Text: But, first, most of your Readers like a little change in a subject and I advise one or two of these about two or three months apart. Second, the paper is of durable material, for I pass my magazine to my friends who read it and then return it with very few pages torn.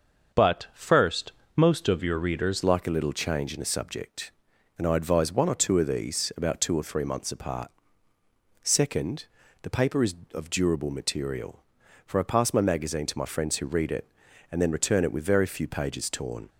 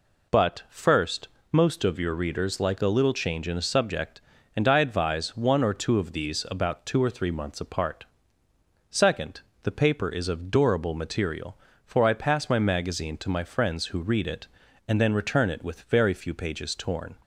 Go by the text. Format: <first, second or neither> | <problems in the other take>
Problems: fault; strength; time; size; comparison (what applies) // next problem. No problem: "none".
second | starts louder than the rest; noticeable; until 1.6 s; 6 dB // changes voice at "like"; from 2.6 s on; 13.8 s long